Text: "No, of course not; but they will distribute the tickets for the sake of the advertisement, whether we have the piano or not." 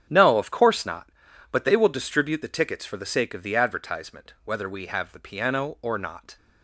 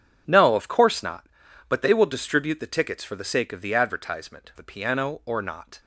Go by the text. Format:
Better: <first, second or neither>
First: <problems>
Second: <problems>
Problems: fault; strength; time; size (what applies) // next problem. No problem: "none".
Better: first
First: starts louder than the rest; strong; until 1.1 s; 8.5 dB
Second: starts louder than the rest; strong; until 1.2 s; 8 dB // skips "whether we have"; at 4.5 s